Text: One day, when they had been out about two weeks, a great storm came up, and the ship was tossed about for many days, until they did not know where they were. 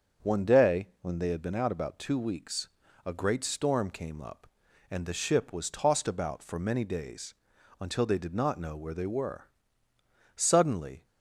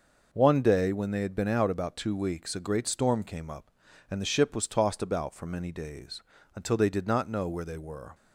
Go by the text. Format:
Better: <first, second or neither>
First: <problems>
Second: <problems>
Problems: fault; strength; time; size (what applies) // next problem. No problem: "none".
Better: second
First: starts louder than the rest; until 1.3 s; 6.5 dB // goes on to say "Suddenly"; noticeable; from 10.3 s on; 0.70 s long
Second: none